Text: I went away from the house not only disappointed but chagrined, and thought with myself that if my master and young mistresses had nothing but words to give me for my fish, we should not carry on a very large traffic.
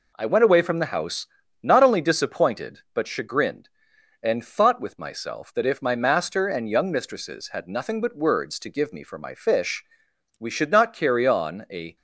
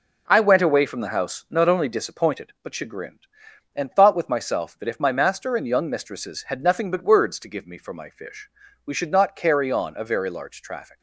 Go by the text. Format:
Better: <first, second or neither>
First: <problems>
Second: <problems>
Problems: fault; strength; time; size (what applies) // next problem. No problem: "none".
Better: second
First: pauses between "house" and "not"; slight; at 1.2 s; 0.36 s long // stops before "very large traffic"; at 11.9 s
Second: none